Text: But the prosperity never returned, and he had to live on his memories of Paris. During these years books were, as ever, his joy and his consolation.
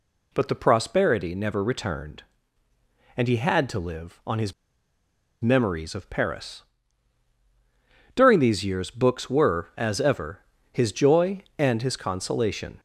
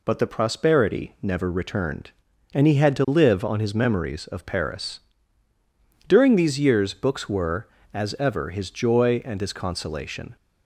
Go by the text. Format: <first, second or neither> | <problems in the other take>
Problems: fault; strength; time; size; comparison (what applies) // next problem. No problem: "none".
second | pauses between "his" and "memories"; noticeable; at 4.5 s; 0.88 s long